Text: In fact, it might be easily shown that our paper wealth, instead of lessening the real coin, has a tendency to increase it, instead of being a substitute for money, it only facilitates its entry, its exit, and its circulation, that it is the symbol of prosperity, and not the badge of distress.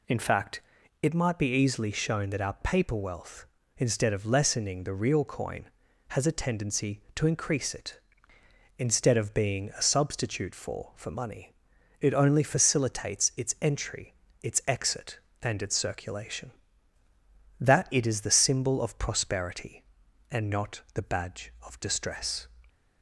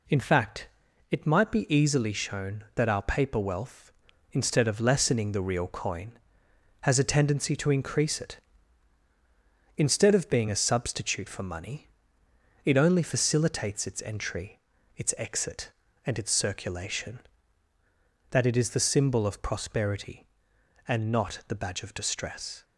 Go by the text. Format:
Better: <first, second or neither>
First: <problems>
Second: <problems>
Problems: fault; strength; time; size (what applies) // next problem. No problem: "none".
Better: second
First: says "for" twice; at 10.9 s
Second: none